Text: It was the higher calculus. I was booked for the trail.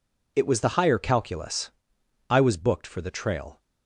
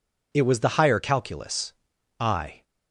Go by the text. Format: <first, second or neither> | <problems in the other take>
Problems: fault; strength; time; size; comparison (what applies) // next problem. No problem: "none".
first | stops before "was booked for the trail"; at 2.6 s